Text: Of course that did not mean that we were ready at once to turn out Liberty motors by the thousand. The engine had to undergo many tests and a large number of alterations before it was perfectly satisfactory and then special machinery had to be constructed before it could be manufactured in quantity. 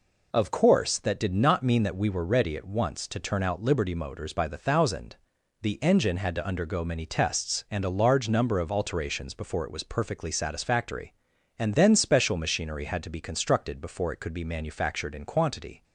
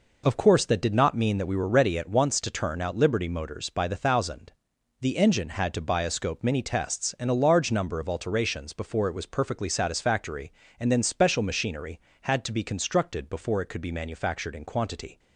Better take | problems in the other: first | says "bioscope" for "undergo"; at 5.8 s

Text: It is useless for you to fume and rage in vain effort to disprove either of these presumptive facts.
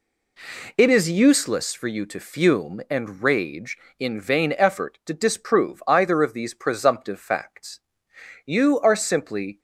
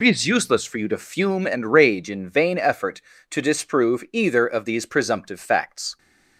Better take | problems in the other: second | goes on to say "You are simply"; noticeable; from 8.4 s on; 1.1 s long

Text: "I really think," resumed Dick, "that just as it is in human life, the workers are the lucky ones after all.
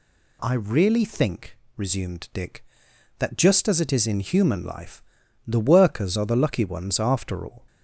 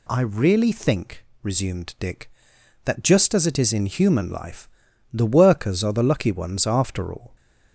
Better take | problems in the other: neither | none

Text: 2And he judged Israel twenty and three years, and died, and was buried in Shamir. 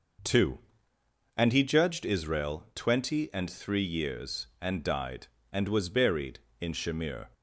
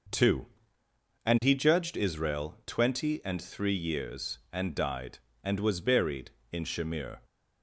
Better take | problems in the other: neither | none

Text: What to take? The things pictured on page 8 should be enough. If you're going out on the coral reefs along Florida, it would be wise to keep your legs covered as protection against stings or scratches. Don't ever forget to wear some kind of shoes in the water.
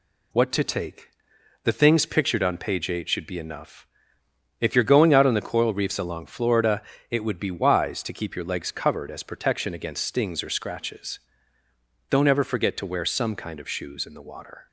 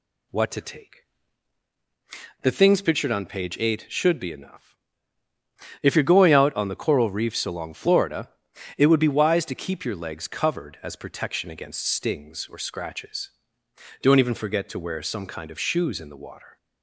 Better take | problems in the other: first | says "even" for "ever"; at 14.1 s

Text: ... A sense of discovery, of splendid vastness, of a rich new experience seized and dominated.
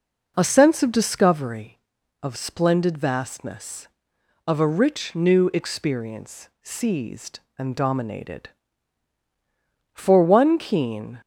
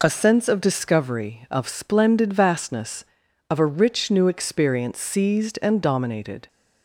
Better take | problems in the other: second | goes on to say "For one keen"; noticeable; from 9.9 s on; 1.2 s long

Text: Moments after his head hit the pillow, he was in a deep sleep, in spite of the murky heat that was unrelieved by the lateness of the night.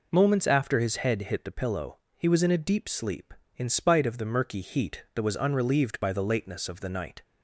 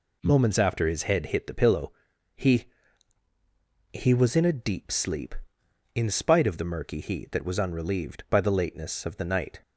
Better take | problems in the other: first | says "he" twice; at 3.9 s

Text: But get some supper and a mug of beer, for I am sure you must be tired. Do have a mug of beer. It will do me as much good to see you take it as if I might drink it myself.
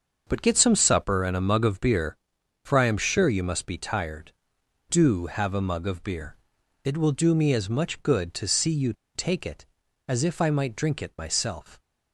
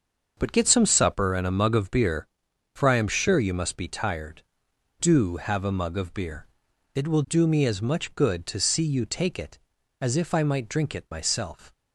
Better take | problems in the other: second | starts louder than the rest; until 1.2 s; 6.5 dB; also in the second // pauses between "you" and "take"; slight; at 8.9 s; 0.21 s long

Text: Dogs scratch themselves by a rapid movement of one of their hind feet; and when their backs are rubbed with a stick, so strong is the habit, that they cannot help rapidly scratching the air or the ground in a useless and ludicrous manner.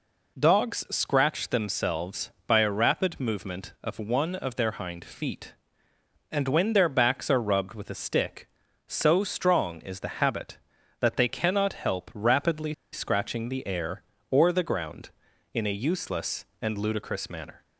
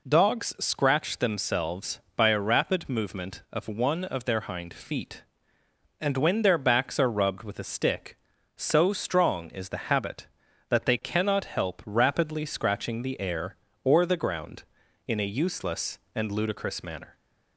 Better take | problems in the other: second | pauses between "rapidly" and "scratching"; slight; at 12.7 s; 0.20 s long

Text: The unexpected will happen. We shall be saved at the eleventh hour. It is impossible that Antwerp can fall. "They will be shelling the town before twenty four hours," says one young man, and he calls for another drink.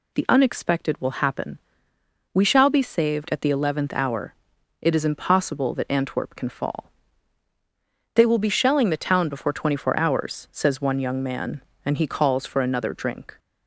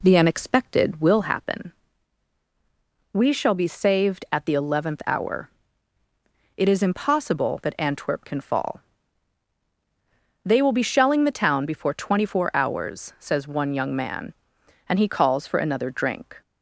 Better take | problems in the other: first | starts louder than the rest; slight; until 1.3 s; 2 dB

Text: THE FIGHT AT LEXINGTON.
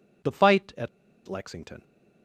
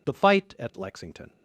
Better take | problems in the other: second | pauses between "AT" and "LEXINGTON"; at 0.8 s; 0.38 s long

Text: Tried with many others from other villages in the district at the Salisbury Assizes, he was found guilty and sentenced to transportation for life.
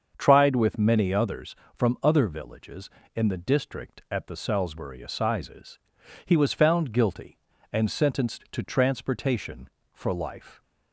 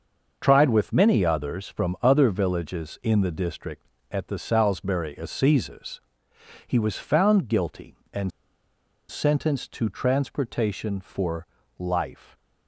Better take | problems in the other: first | starts louder than the rest; until 1.4 s; 6 dB; also in the first // pauses between "and" and "sentenced"; noticeable; at 8.3 s; 0.79 s long // pauses between "for" and "life"; slight; at 11.4 s; 0.32 s long

